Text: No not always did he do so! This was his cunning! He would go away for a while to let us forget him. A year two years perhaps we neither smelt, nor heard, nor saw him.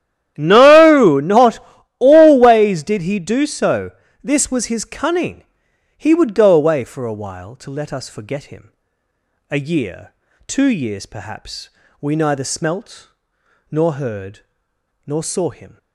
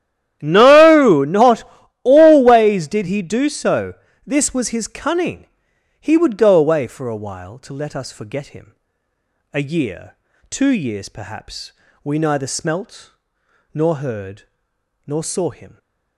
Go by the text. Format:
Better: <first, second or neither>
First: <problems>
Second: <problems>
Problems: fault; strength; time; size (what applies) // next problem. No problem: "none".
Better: neither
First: starts louder than the rest; strong; until 1.3 s; 11.5 dB // pauses between "not" and "always"; at 1.5 s; 0.40 s long // pauses between "year" and "two"; slight; at 10.1 s; 0.36 s long // pauses between "perhaps" and "we"; slight; at 11.6 s; 0.32 s long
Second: starts louder than the rest; strong; until 1.4 s; 11.5 dB // pauses between "not" and "always"; at 1.6 s; 0.40 s long // pauses between "year" and "two"; slight; at 10.1 s; 0.36 s long // pauses between "perhaps" and "we"; slight; at 11.7 s; 0.32 s long